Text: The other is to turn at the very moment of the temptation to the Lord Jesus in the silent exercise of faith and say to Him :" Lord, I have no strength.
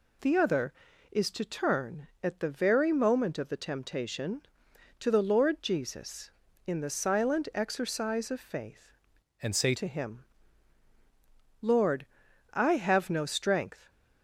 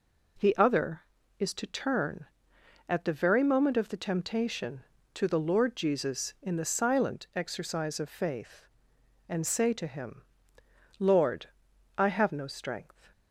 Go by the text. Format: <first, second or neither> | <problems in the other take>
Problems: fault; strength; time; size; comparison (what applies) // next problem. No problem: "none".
second | changes voice from "and" to "say"; from 9.4 to 9.7 s; 0.3 s long